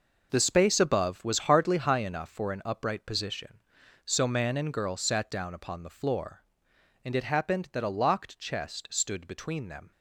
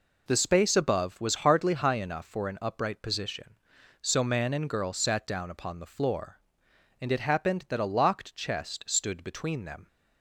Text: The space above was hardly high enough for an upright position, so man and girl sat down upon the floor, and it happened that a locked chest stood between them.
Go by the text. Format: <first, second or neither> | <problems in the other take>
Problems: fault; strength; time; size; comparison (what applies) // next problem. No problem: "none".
second | gets quieter; strong; throughout; 9.5 dB